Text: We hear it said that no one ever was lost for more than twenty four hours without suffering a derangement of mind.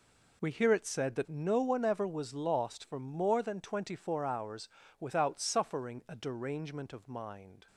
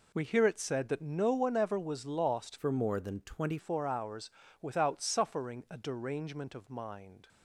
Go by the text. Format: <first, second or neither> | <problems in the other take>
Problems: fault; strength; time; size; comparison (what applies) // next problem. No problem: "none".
first | changes voice from "for" to "twenty"; from 2.5 to 3.5 s; 1.0 s long // pauses between "hours" and "without"; slight; at 4.3 s; 0.30 s long; slight in the first